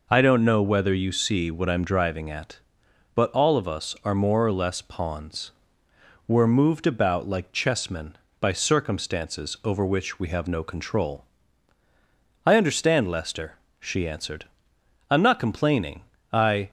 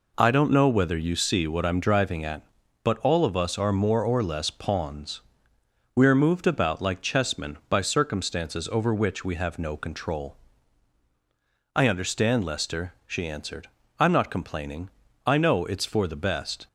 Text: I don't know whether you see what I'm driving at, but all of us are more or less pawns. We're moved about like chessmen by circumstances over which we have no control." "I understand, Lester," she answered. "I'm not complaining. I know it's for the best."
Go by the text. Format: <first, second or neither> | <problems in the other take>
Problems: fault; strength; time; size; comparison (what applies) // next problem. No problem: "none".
second | stops before "know it's for the best"; at 16.6 s